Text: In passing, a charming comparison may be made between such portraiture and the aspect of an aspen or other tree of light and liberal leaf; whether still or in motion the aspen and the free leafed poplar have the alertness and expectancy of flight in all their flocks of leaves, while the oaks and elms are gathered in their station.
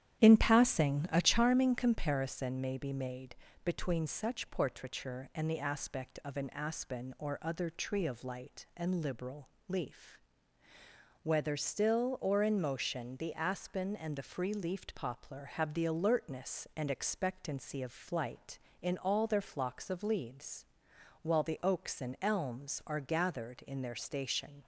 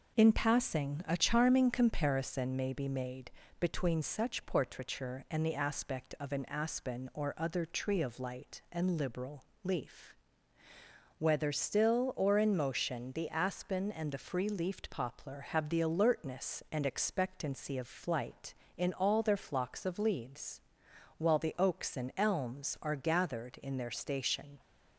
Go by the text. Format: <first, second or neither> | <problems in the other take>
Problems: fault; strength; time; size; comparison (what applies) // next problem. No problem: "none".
second | starts louder than the rest; strong; until 1.5 s; 10.5 dB // pauses between "made" and "between"; slight; at 3.3 s; 0.28 s long; slight in the second // pauses between "liberal" and "leaf"; slight; at 9.4 s; 0.20 s long; slight in the second